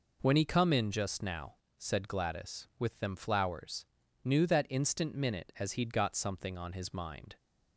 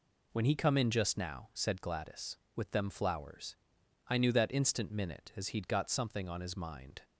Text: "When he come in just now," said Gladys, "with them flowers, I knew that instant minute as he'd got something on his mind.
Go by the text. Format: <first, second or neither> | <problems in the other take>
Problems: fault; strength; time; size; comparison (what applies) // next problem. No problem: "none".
second | skips "I"; at 4.0 s